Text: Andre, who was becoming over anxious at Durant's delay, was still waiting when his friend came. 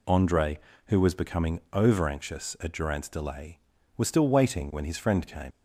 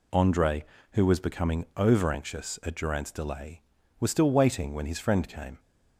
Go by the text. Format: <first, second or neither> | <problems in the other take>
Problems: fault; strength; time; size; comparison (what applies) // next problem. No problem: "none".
second | leaves "came" unfinished; at 5.5 s; 70 ms